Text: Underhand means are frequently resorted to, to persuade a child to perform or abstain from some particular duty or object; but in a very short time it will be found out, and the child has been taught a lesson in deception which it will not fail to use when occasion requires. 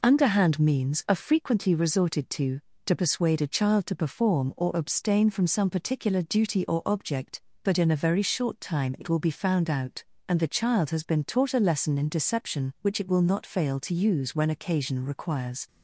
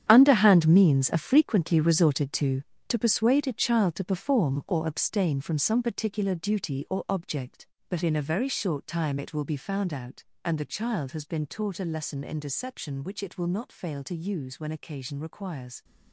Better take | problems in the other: first | gets quieter; strong; throughout; 12.5 dB

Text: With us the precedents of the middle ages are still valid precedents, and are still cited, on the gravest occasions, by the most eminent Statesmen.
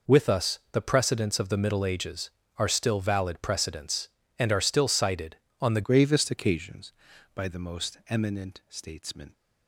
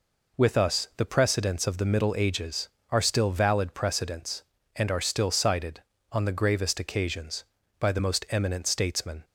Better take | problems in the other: second | changes voice at "gravest"; from 5.8 s on; 3.5 s long

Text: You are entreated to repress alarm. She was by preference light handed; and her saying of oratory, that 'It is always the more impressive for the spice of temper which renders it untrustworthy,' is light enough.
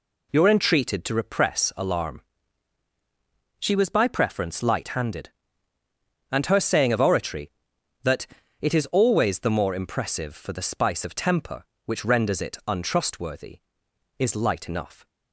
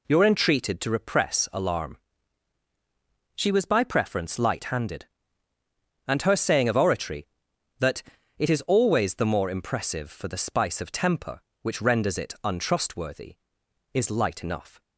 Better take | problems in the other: neither | pauses between "that" and "It"; slight; the same in both

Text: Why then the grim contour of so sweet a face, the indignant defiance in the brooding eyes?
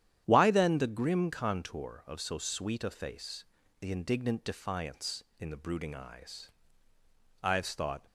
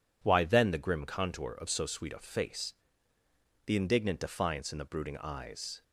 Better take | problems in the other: second | starts louder than the rest; strong; until 1.2 s; 10.5 dB // goes on to say "Ives thought"; noticeable; from 7.4 s on; 0.64 s long

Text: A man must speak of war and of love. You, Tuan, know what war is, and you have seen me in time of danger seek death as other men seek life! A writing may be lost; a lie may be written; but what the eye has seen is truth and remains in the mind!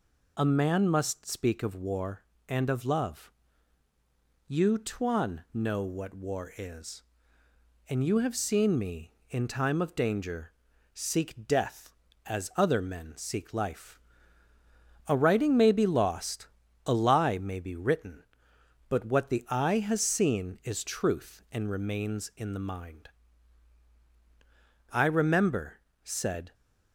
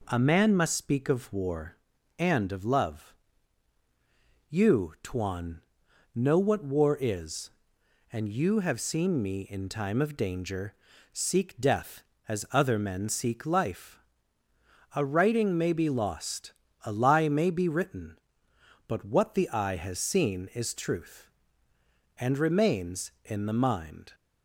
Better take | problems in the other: second | pauses between "danger" and "seek"; at 10.5 s; 0.40 s long; also in the second // goes on to say "I remember said"; from 24.9 s on; 1.6 s long

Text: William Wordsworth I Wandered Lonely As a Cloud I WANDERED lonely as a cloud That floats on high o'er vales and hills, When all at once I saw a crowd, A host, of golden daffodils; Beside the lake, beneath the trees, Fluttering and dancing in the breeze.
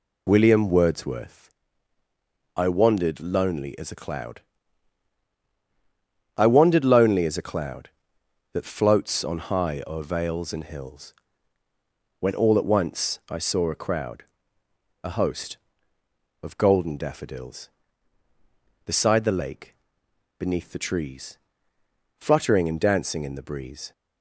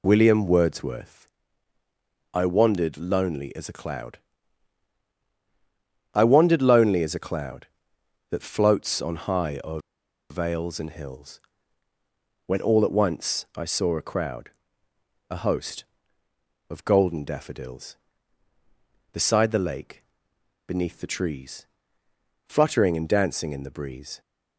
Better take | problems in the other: first | pauses between "Wordsworth" and "I"; at 1.3 s; 1.0 s long; also in the first // pauses between "Cloud" and "I"; strong; at 4.1 s; 1.9 s long; strong in the first // pauses between "o'er" and "vales"; noticeable; at 9.7 s; 0.50 s long

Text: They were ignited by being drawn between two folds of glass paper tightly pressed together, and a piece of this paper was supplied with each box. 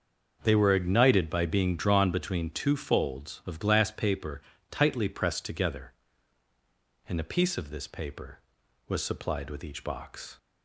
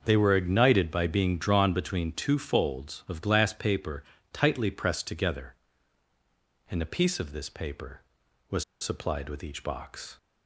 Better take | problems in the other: first | starts louder than the rest; until 1.0 s; 6.5 dB; also in the first // pauses between "paper" and "tightly"; slight; at 4.0 s; 0.30 s long; slight in the first // pauses between "was" and "supplied"; slight; at 8.6 s; 0.17 s long

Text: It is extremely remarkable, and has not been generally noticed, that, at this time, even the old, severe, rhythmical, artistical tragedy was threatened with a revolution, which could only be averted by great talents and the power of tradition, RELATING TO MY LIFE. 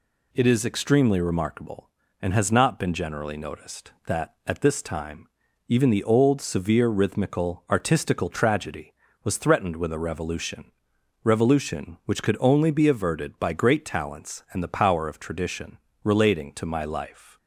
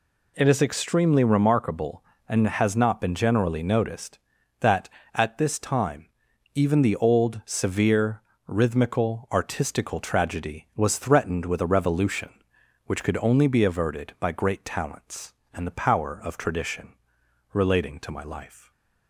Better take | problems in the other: second | says "revolution" twice; at 11.2 s

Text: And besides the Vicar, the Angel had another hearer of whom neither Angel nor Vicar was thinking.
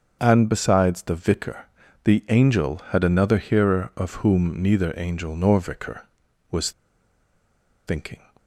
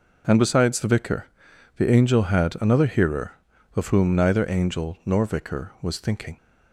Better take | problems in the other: second | starts louder than the rest; until 1.2 s; 6.5 dB // pauses between "was" and "thinking"; at 6.7 s; 1.1 s long

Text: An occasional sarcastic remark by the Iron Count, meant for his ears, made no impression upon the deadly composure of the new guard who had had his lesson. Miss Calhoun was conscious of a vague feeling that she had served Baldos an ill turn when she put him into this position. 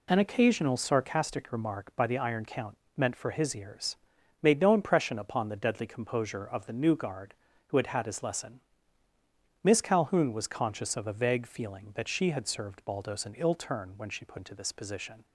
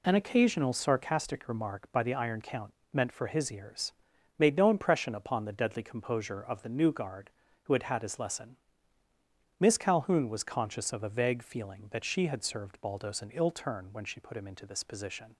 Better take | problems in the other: second | skips "him"; at 14.3 s

